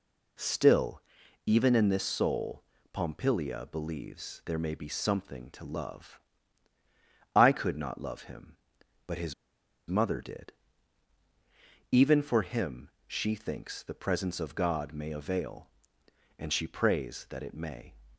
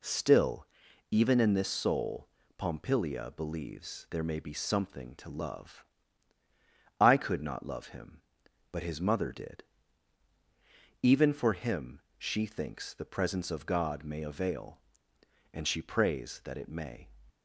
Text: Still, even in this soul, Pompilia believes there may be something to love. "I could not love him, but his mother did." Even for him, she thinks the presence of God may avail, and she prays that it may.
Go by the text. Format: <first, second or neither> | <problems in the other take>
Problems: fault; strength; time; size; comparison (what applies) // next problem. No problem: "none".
second | pauses between "his" and "mother"; noticeable; at 9.3 s; 0.56 s long